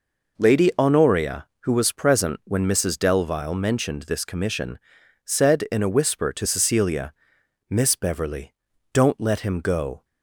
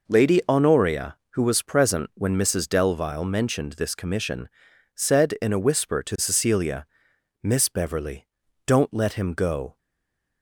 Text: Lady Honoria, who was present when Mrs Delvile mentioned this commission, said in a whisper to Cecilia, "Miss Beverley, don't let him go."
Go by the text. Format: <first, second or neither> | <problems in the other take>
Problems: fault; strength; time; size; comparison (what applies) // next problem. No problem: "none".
first | stays silent after the last word; slight; from 9.7 s on; 0.7 s long